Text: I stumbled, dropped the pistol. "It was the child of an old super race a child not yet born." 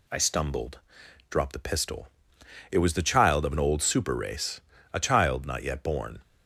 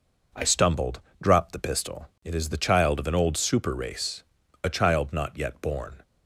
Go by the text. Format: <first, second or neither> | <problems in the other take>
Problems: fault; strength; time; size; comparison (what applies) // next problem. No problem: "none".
first | says "is" for "was"; at 2.3 s // pauses between "race" and "a"; at 4.2 s; 0.42 s long; slight in the first